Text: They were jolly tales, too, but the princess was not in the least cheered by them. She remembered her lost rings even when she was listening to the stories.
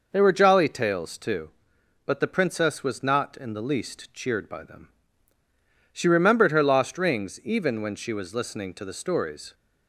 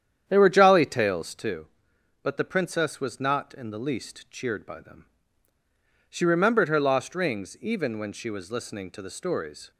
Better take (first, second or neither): first